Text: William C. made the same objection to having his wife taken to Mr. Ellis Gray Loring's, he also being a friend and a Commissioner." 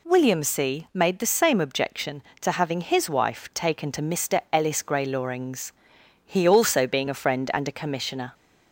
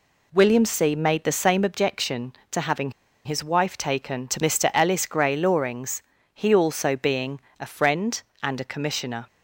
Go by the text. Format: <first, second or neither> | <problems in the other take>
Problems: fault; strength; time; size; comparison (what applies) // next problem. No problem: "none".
first | pauses between "having" and "his"; slight; at 2.9 s; 0.33 s long // pauses between "being" and "a"; slight; at 7.4 s; 0.18 s long